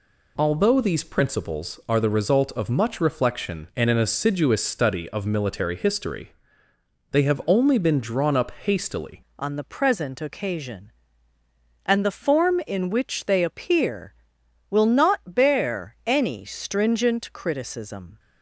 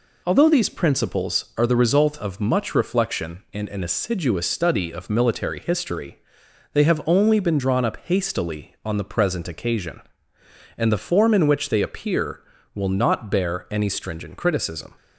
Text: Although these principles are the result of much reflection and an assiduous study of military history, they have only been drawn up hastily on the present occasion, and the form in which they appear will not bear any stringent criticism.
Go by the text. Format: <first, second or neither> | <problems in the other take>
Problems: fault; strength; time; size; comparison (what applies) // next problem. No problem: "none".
second | changes voice at "on"; from 9.3 s on; 8.8 s long